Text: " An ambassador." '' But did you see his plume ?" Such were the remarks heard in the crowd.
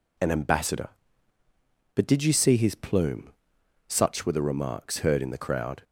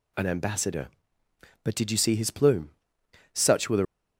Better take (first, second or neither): first